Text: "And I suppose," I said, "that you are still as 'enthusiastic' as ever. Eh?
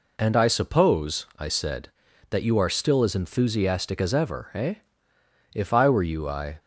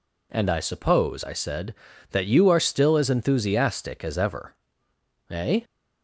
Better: second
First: goes on to say "If I were you I"; noticeable; from 5.5 s on; 1.0 s long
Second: none

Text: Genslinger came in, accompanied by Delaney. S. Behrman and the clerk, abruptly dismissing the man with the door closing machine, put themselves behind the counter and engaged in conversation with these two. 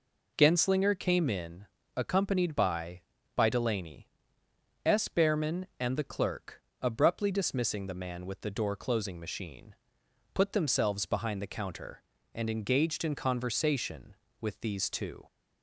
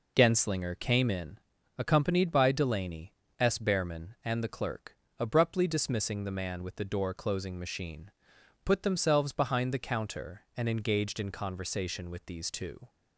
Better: second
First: says "by" twice; at 3.3 s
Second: none

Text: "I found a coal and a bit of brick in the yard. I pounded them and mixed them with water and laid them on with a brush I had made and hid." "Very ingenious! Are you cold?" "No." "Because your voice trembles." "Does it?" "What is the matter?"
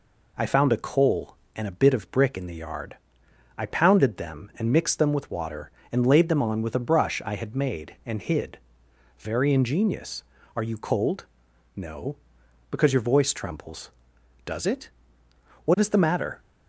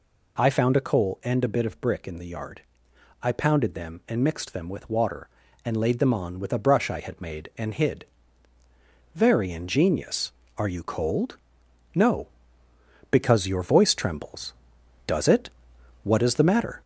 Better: first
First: none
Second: gets louder; throughout; 3.5 dB

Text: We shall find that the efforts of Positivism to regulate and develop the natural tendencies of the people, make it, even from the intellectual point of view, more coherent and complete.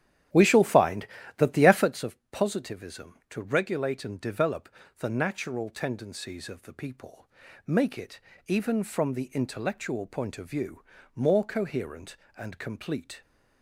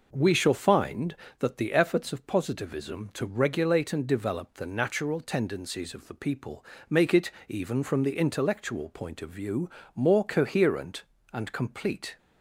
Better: second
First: starts louder than the rest; strong; until 2.2 s; 11 dB // pauses between "develop" and "the"; slight; at 4.6 s; 0.30 s long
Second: none

